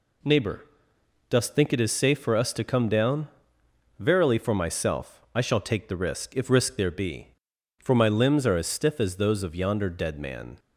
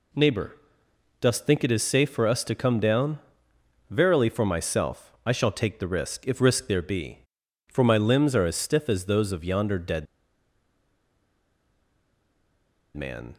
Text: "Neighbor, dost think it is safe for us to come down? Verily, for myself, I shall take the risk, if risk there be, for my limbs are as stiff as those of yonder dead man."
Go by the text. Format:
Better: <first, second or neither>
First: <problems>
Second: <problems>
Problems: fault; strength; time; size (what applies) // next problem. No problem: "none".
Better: first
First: none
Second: pauses between "dead" and "man"; strong; at 10.0 s; 2.9 s long